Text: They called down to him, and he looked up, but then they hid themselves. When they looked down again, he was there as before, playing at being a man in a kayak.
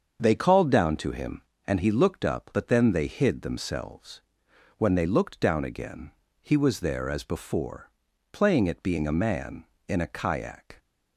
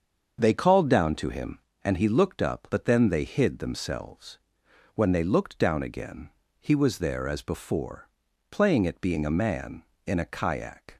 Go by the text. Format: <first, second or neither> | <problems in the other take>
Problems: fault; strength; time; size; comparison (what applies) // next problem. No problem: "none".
neither | starts louder than the rest; the same in both